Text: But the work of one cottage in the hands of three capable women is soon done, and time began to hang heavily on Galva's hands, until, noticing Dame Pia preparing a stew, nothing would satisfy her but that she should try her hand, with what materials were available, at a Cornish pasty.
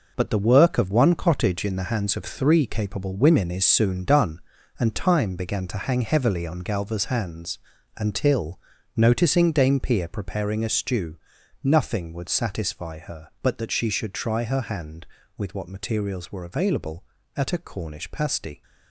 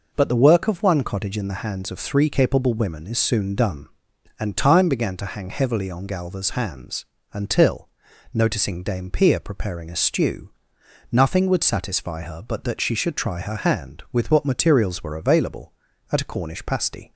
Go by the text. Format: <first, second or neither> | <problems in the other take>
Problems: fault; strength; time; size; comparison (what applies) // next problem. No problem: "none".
second | gets quieter; strong; throughout; 8.5 dB